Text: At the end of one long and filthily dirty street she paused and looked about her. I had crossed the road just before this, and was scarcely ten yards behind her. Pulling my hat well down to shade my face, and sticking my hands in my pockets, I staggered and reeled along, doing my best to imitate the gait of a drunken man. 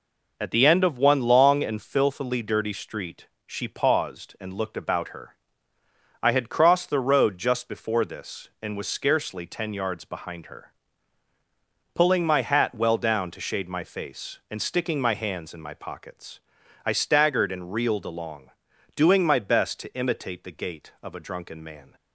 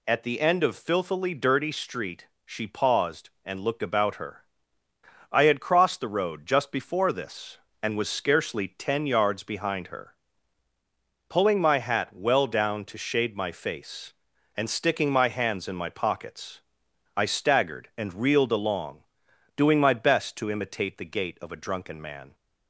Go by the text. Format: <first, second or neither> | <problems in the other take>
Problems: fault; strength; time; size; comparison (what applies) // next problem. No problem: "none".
first | skips "one long and"; at 0.7 s // pauses between "street" and "she"; slight; at 2.2 s; 0.18 s long; slight in the first